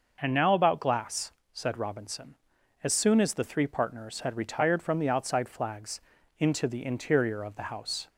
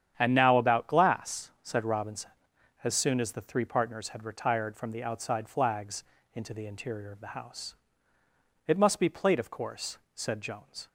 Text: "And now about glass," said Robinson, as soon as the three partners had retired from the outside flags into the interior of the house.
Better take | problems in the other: first | starts louder than the rest; strong; until 1.1 s; 9 dB // pauses between "flags" and "into"; slight; at 6.0 s; 0.30 s long; also in the first // goes on to say "It must be plate of course said Jones"; strong; from 8.6 s on; 2.2 s long

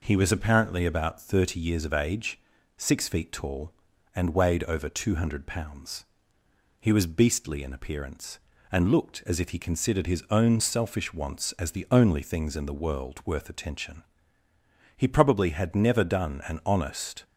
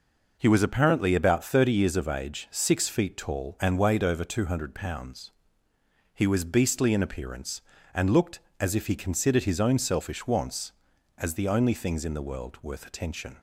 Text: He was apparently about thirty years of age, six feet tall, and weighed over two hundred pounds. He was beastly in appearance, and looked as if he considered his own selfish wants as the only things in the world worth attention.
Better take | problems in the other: second | goes on to say "He probably had never done an honest"; strong; from 14.9 s on; 2.2 s long

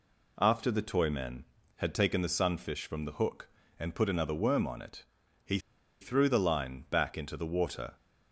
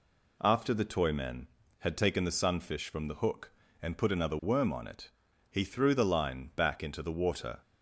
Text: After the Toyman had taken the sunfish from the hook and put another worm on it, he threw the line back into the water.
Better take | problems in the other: second | pauses between "he" and "threw"; at 5.5 s; 0.42 s long

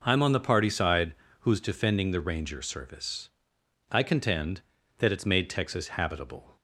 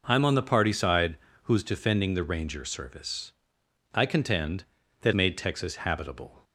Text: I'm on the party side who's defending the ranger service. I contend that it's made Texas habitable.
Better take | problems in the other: first | pauses between "side" and "who's"; slight; at 1.1 s; 0.28 s long; slight in the first // skips "it's"; at 5.1 s

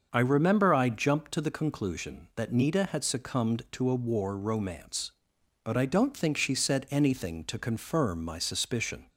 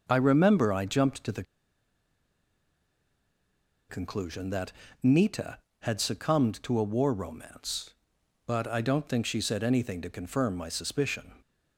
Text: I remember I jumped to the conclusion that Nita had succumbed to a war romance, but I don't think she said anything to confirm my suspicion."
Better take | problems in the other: first | starts louder than the rest; noticeable; until 1.0 s; 6 dB; also in the first // pauses between "the" and "conclusion"; strong; at 1.4 s; 2.4 s long // pauses between "that" and "Nita"; slight; at 4.7 s; 0.32 s long

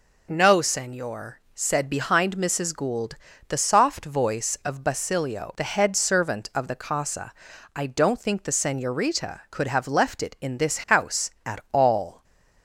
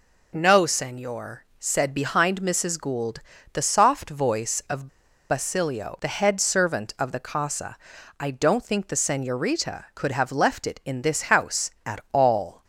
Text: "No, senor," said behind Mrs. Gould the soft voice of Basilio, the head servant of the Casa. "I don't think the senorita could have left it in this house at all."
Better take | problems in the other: first | pauses between "Gould" and "the"; slight; at 3.1 s; 0.32 s long; slight in the first // pauses between "of" and "Basilio"; at 4.8 s; 0.41 s long

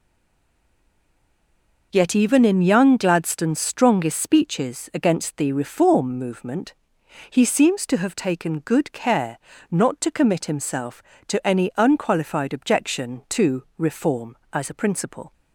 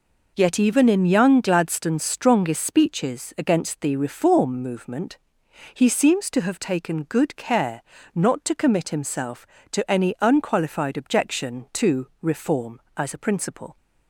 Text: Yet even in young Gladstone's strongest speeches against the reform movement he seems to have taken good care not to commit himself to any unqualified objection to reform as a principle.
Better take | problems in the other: second | stays silent before the first word; noticeable; until 1.9 s; 1.9 s long // pauses between "movement" and "he"; noticeable; at 6.7 s; 0.56 s long; noticeable in the second // pauses between "care" and "not"; slight; at 9.3 s; 0.32 s long; slight in the second

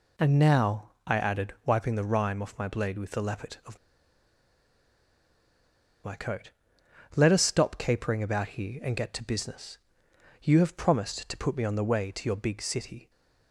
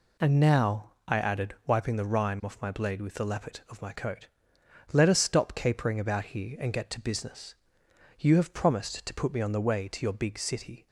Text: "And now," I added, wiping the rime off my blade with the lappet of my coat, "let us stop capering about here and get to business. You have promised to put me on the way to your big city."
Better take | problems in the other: second | pauses between "of" and "my"; strong; at 3.7 s; 2.2 s long

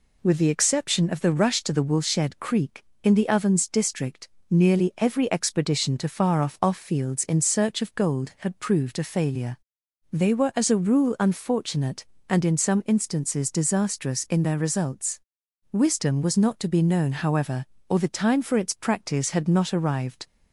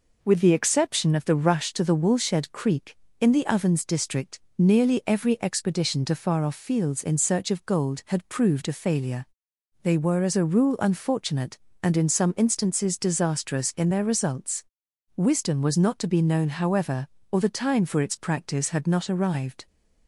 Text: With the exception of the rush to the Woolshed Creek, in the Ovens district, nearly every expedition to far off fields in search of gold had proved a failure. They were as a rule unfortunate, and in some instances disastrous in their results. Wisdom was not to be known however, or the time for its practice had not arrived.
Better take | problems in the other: second | says "off" twice; at 6.6 s

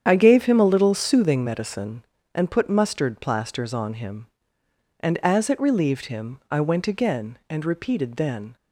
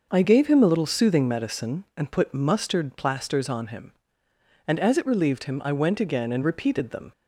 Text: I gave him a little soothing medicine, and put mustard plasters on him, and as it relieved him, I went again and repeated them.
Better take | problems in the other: second | starts louder than the rest; strong; until 1.1 s; 8.5 dB // says "then" for "them"; at 8.1 s

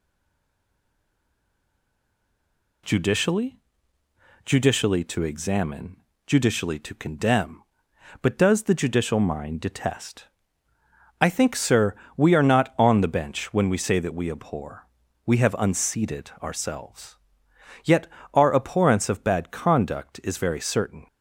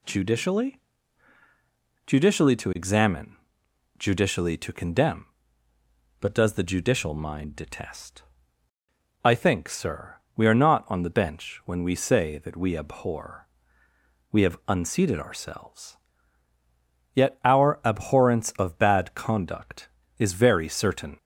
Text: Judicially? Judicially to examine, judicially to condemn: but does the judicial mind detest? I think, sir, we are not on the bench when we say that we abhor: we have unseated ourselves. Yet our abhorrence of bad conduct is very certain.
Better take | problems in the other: second | stays silent before the first word; strong; until 2.8 s; 2.8 s long // pauses between "Yet" and "our"; slight; at 18.0 s; 0.26 s long

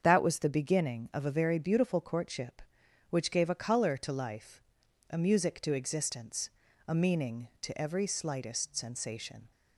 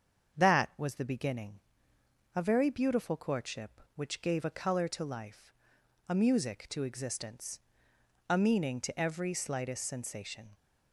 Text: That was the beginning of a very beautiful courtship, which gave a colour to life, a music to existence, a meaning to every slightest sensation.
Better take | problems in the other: first | starts louder than the rest; strong; until 1.4 s; 7.5 dB; strong in the first // skips "of"; at 1.9 s

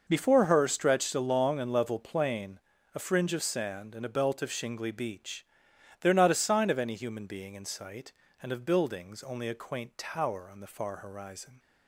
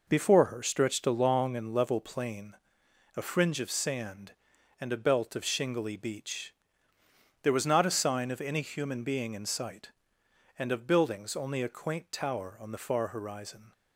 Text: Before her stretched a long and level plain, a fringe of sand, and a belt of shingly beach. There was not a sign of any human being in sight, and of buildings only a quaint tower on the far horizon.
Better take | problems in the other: second | skips "was"; at 6.1 s

